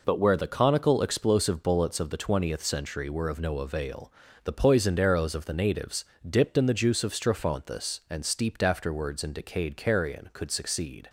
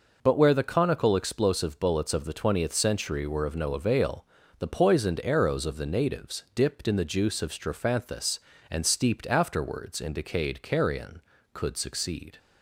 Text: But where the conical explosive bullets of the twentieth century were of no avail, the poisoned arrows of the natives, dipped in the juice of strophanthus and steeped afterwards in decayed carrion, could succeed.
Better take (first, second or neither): neither